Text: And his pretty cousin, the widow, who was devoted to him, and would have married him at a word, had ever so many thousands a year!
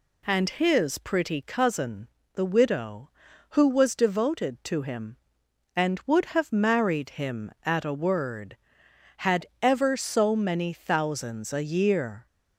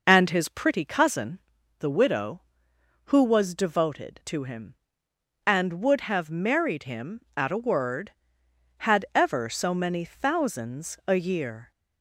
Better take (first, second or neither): first